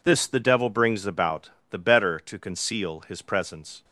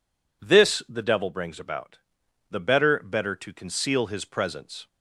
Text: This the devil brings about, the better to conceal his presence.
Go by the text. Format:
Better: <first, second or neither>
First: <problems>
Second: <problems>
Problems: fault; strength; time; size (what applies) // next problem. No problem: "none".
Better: first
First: none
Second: says "better" twice; at 2.9 s